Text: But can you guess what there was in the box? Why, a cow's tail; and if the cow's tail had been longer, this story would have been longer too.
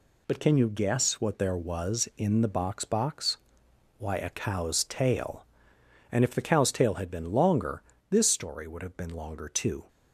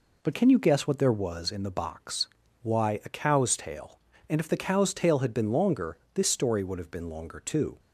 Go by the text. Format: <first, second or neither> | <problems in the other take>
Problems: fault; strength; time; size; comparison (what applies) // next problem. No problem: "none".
second | says "box" twice; at 2.8 s